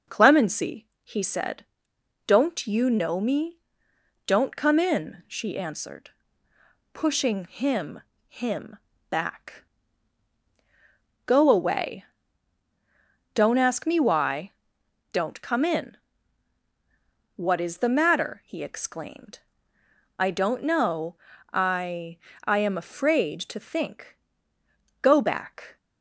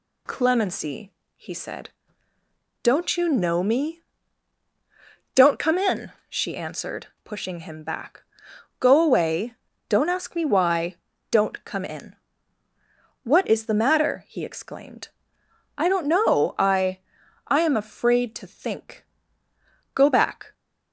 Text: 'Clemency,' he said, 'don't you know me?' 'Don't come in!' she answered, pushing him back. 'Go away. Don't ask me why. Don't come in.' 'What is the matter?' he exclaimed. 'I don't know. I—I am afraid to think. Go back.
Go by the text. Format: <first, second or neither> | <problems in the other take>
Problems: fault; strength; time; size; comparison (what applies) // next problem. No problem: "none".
second | says "him" twice; at 8.2 s